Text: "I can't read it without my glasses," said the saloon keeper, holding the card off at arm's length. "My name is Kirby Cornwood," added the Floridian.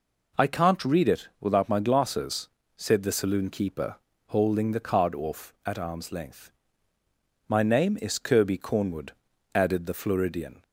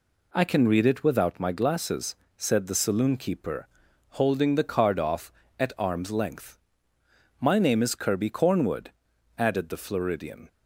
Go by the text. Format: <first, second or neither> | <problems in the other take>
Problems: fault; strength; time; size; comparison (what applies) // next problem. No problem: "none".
first | says "can" for "can't"; at 0.4 s